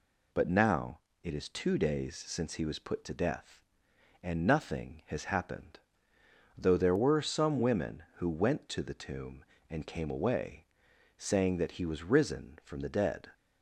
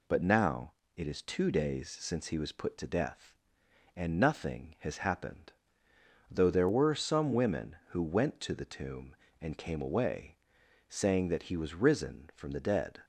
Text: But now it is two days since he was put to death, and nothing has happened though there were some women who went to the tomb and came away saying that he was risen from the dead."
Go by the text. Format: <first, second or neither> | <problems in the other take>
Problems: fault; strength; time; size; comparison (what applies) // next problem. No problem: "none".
neither | pauses between "now" and "it"; slight; the same in both // pauses between "happened" and "though"; noticeable; the same in both // pauses between "away" and "saying"; noticeable; the same in both